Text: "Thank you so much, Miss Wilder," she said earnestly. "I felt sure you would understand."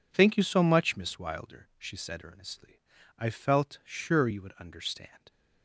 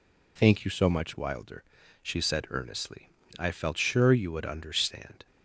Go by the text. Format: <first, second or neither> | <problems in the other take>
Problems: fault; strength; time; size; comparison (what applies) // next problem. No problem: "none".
first | skips "Miss"; at 1.1 s